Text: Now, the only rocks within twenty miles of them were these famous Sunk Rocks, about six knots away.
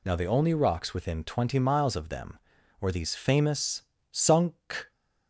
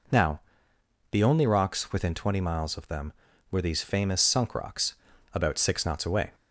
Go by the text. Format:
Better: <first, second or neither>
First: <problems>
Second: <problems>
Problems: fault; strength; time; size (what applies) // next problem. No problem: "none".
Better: second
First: pauses between "famous" and "Sunk"; slight; at 3.8 s; 0.28 s long // stops before "Rocks about six knots away"; at 4.9 s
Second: none